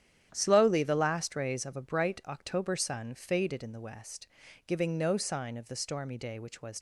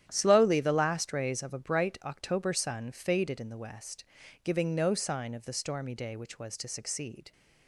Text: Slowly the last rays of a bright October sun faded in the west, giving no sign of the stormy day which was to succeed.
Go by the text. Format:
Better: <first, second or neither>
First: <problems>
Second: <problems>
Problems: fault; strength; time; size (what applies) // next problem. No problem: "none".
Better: second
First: starts louder than the rest; strong; until 1.3 s; 10.5 dB // stops before "to succeed"; at 6.7 s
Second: starts louder than the rest; strong; until 1.1 s; 10.5 dB